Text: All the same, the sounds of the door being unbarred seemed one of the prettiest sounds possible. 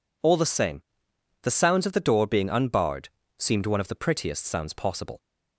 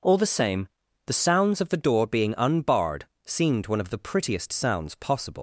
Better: first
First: pauses between "unbarred" and "seemed"; slight; at 3.0 s; 0.30 s long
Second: pauses between "unbarred" and "seemed"; slight; at 3.0 s; 0.20 s long // leaves "possible" unfinished; at 5.3 s; 135 ms

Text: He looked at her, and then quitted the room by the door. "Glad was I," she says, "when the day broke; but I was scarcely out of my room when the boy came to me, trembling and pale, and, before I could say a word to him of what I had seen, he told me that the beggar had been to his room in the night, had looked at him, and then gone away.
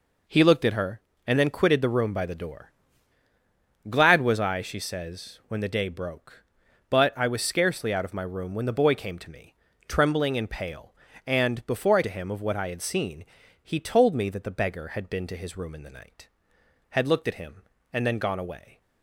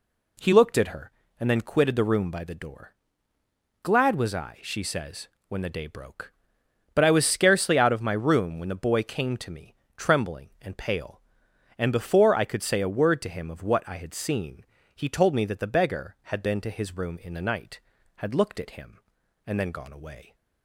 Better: second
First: skips "could say a word"; at 12.0 s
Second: none

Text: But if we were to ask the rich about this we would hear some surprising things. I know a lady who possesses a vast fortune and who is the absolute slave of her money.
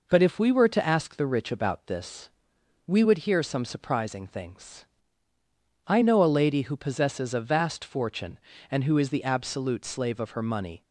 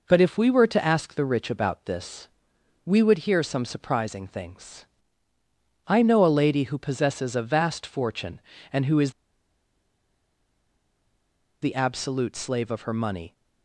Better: first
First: pauses between "this" and "we"; noticeable; at 2.2 s; 0.58 s long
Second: pauses between "this" and "we"; noticeable; at 2.2 s; 0.58 s long // pauses between "is" and "the"; strong; at 9.1 s; 2.5 s long

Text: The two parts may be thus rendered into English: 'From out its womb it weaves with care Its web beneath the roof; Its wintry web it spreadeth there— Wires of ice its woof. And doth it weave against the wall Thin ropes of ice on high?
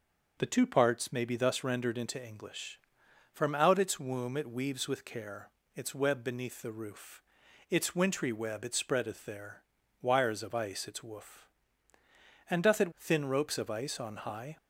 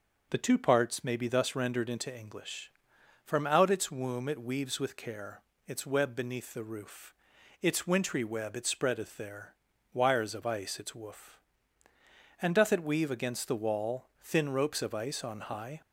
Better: second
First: starts louder than the rest; noticeable; until 1.4 s; 6 dB // pauses between "care" and "Its"; slight; at 5.5 s; 0.26 s long // skips "weave against the wall"; at 12.9 s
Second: starts louder than the rest; noticeable; until 1.3 s; 6 dB // pauses between "care" and "Its"; slight; at 5.4 s; 0.26 s long

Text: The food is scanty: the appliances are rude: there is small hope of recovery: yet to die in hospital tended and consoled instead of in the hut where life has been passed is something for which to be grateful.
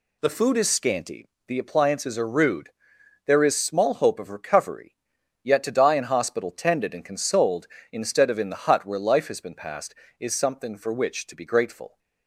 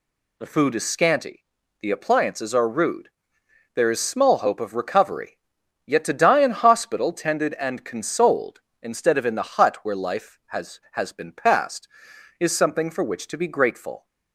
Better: first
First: none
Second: says "has" twice; at 10.9 s

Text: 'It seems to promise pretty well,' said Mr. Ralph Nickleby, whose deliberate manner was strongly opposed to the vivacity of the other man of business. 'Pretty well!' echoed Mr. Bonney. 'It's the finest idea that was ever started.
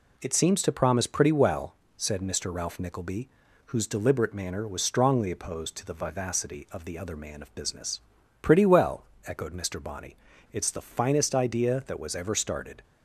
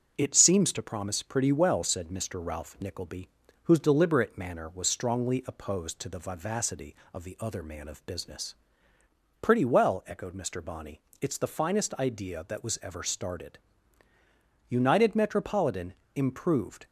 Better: first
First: none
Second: starts louder than the rest; until 1.1 s; 6.5 dB // goes on to say "United Metropolitan Improved"; strong; from 14.6 s on; 2.1 s long

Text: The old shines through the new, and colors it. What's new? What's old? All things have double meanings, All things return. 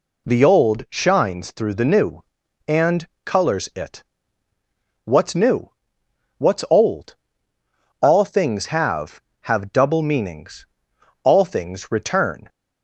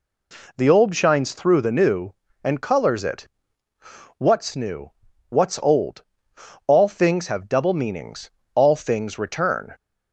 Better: second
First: pauses between "and" and "colors"; slight; at 3.0 s; 0.20 s long // says "have" twice; at 9.4 s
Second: none

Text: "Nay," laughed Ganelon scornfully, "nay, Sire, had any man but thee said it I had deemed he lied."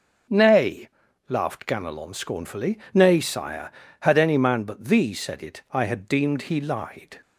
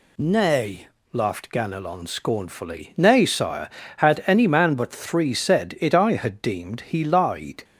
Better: first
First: none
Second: says "three" for "thee"; at 4.8 s

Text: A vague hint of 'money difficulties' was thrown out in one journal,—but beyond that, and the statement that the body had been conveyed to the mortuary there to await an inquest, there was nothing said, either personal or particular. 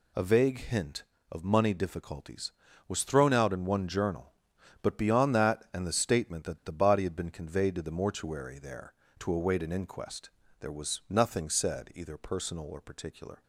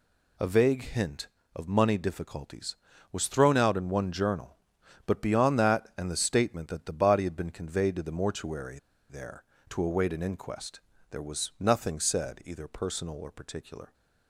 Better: first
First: none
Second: pauses between "mortuary" and "there"; slight; at 8.7 s; 0.30 s long

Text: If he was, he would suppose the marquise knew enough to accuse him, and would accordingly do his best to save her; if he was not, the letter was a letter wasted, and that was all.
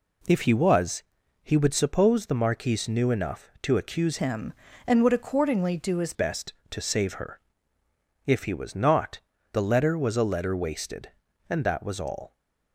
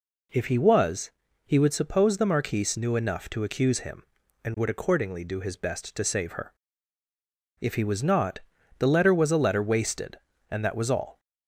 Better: second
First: changes voice from "him" to "his"; from 4.1 to 6.1 s; 2.0 s long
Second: none

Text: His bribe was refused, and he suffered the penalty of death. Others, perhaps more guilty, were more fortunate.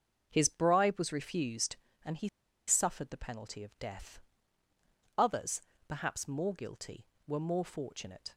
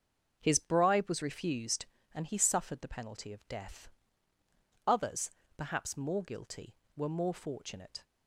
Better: second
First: starts louder than the rest; until 1.3 s; 6.5 dB // pauses between "he" and "suffered"; at 2.2 s; 0.39 s long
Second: starts louder than the rest; until 1.4 s; 6.5 dB

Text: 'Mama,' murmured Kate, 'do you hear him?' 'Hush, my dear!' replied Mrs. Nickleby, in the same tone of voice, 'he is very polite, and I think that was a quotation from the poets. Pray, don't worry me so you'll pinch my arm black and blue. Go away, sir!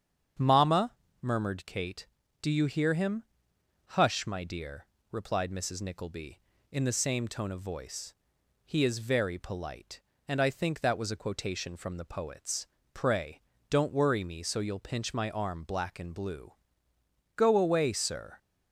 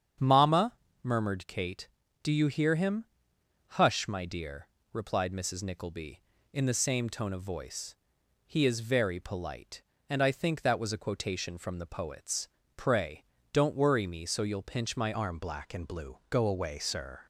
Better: first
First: starts louder than the rest; strong; until 1.6 s; 8 dB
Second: starts louder than the rest; strong; until 1.4 s; 8 dB // changes voice at "arm"; from 15.1 s on; 2.1 s long

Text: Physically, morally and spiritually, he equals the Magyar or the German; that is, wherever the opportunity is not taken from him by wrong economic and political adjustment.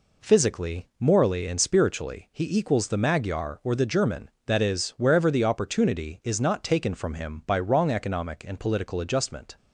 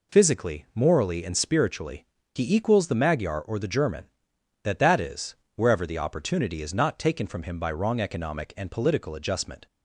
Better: first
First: none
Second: says "that" twice; at 4.8 s

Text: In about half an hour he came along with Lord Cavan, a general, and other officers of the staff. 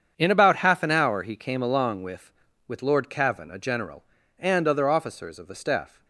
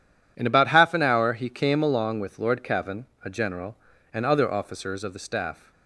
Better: second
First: starts louder than the rest; strong; until 1.1 s; 7.5 dB // says "with" twice; at 2.6 s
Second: none

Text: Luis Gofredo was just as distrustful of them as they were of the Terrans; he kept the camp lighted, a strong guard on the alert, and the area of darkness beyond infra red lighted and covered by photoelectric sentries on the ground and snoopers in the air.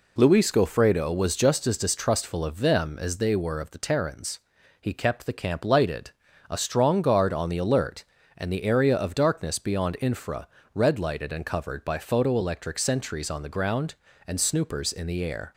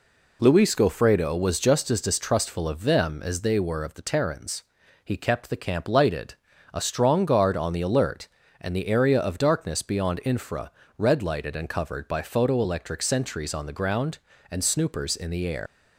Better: first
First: pauses between "infra" and "red"; slight; at 10.4 s; 0.26 s long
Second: pauses between "infra" and "red"; slight; at 10.7 s; 0.26 s long // leaves "air" unfinished; at 15.6 s; 105 ms

